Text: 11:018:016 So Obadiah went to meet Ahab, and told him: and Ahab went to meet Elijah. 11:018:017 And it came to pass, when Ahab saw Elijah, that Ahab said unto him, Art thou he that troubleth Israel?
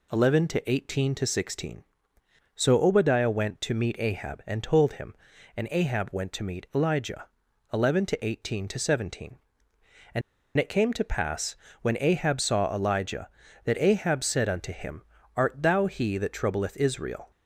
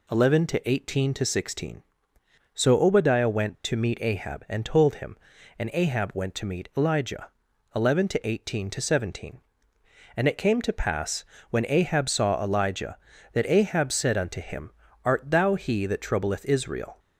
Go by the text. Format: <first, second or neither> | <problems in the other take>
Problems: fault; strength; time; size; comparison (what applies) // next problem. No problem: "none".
second | pauses between "And" and "it"; at 10.2 s; 0.36 s long